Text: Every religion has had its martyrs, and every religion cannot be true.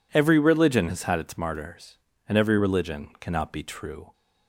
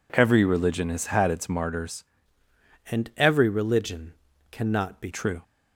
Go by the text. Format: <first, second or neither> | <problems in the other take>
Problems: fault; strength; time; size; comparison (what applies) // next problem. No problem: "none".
first | changes voice from "and" to "be"; from 2.8 to 5.0 s; 2.2 s long // pauses between "religion" and "cannot"; at 4.1 s; 0.38 s long